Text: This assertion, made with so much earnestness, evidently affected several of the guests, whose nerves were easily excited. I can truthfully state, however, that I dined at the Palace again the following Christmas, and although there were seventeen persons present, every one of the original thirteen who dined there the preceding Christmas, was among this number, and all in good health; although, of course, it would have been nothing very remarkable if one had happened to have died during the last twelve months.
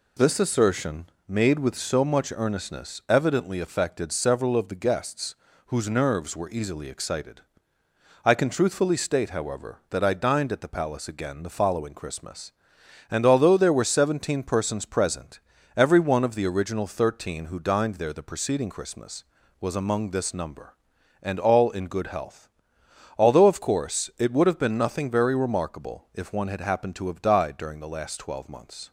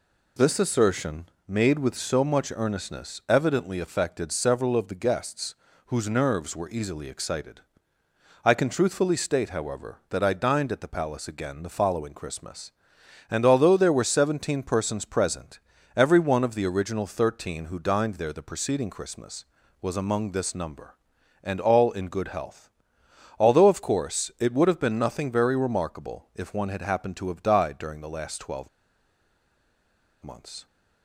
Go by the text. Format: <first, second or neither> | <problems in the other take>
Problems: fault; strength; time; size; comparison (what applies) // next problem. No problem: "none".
first | pauses between "twelve" and "months"; strong; at 28.6 s; 1.5 s long